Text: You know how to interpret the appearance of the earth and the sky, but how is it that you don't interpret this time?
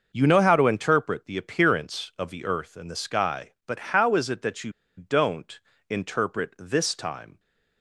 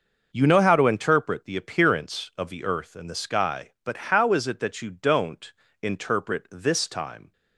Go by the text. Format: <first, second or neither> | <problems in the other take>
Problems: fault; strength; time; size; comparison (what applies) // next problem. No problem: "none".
second | starts louder than the rest; noticeable; until 1.1 s; 6 dB; noticeable in the second // pauses between "you" and "don't"; slight; at 4.7 s; 0.25 s long // pauses between "don't" and "interpret"; slight; at 5.5 s; 0.30 s long; slight in the second